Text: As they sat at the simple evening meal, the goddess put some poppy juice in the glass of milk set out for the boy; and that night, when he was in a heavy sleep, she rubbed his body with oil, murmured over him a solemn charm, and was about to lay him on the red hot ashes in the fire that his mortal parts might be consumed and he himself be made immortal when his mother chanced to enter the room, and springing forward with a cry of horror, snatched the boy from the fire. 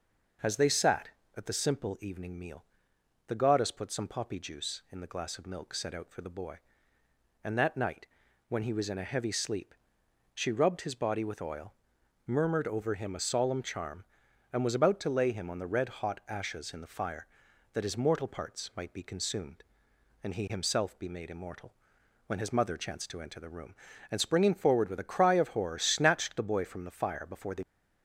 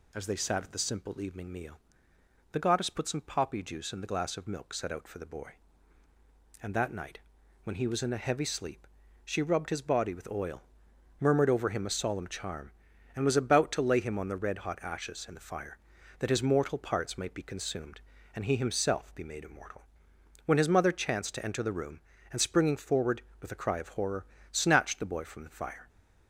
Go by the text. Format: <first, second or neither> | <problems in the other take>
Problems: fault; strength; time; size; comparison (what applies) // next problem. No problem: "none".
second | pauses between "immortal" and "when"; noticeable; at 21.7 s; 0.54 s long; noticeable in the second // goes on to say "Before the"; slight; from 27.2 s on; 0.36 s long